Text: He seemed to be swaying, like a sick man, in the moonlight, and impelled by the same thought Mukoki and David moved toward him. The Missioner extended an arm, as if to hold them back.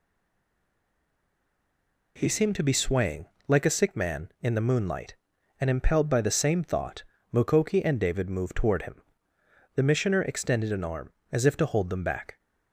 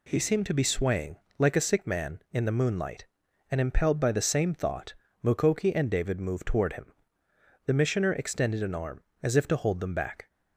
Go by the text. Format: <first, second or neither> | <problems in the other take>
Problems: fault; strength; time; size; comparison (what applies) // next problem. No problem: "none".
second | stays silent before the first word; until 2.1 s; 2.1 s long // pauses between "thought" and "Mukoki"; slight; at 7.0 s; 0.28 s long; slight in the second